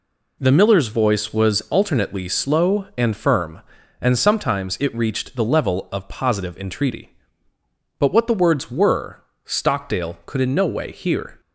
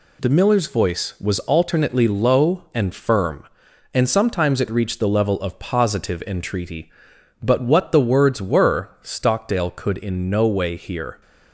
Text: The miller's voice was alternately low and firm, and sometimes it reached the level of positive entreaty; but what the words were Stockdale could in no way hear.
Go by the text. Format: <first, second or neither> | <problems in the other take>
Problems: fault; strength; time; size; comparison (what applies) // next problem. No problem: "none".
second | says "slow" for "low"; at 2.2 s // pauses between "were" and "Stockdale"; slight; at 9.2 s; 0.20 s long